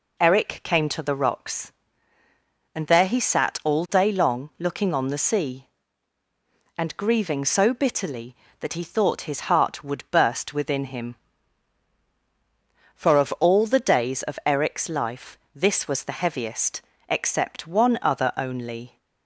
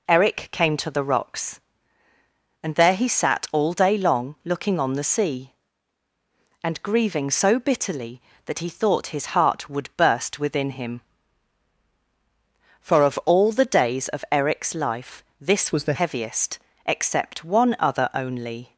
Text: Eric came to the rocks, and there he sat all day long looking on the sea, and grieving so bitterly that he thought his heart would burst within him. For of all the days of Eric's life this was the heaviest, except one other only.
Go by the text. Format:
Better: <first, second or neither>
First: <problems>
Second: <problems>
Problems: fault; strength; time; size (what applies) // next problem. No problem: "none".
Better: first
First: pauses between "life" and "this"; slight; at 15.3 s; 0.16 s long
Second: pauses between "life" and "this"; slight; at 15.2 s; 0.16 s long // changes voice from "was" to "the"; from 15.7 to 15.9 s; 0.2 s long